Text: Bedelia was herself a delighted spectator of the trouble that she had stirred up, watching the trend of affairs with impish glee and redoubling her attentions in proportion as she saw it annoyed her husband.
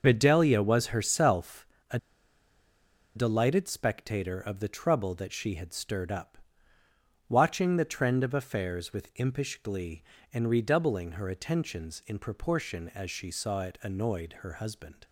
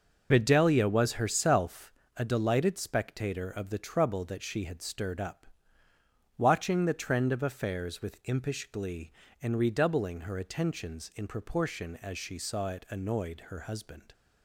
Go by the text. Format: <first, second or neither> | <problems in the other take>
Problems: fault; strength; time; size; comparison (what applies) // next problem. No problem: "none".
second | pauses between "herself" and "a"; slight; at 1.6 s; 0.24 s long; slight in the second // pauses between "a" and "delighted"; at 1.9 s; 1.1 s long